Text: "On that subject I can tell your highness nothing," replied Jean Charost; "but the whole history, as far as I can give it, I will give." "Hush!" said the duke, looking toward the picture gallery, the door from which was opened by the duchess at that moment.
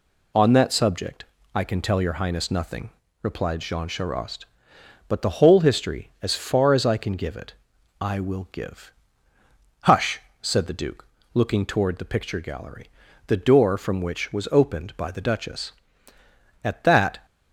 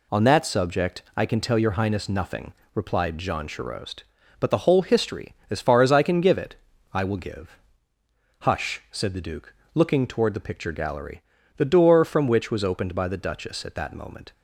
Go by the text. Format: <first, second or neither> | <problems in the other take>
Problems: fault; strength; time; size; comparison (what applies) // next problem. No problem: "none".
second | pauses between "subject" and "I"; slight; at 1.2 s; 0.30 s long; slight in the second // stops before "moment"; at 17.2 s